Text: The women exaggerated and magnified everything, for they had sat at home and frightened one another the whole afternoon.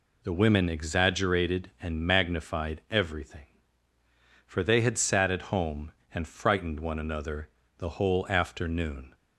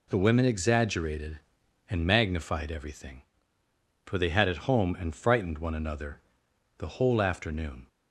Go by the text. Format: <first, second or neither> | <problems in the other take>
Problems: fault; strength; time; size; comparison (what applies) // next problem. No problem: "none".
first | skips "sat"; at 4.4 s // pauses between "another" and "the"; noticeable; at 6.1 s; 0.58 s long; slight in the first